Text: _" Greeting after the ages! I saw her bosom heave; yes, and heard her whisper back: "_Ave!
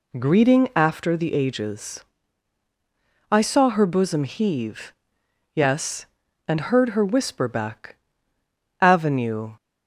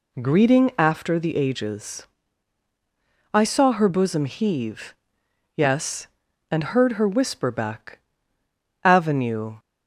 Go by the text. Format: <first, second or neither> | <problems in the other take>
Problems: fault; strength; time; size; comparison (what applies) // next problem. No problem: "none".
neither | none